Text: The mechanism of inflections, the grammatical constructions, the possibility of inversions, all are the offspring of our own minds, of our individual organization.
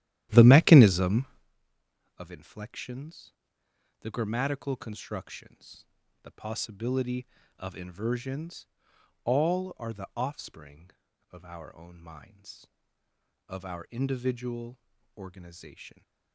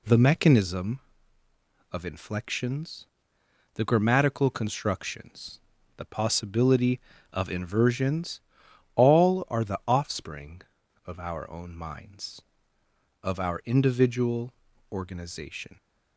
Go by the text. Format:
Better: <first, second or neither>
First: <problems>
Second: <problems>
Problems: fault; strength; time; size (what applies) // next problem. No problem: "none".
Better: second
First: starts louder than the rest; strong; until 1.5 s; 12.5 dB // pauses between "individual" and "organization"; at 14.7 s; 0.40 s long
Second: pauses between "individual" and "organization"; at 14.5 s; 0.40 s long